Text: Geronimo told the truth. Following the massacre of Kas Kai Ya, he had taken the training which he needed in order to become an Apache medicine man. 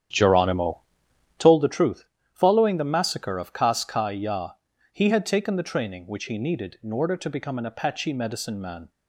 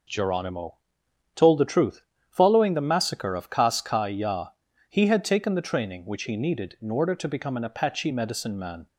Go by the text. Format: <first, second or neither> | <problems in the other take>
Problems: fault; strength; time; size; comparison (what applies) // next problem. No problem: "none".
second | starts louder than the rest; strong; until 1.5 s; 9.5 dB // pauses between "Geronimo" and "told"; noticeable; at 0.7 s; 0.58 s long; noticeable in the second